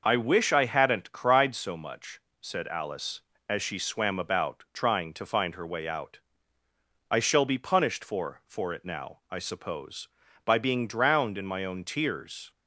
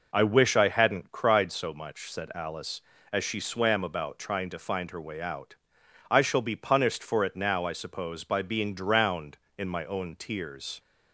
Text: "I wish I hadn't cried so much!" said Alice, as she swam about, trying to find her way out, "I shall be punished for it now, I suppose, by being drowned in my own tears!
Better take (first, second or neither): second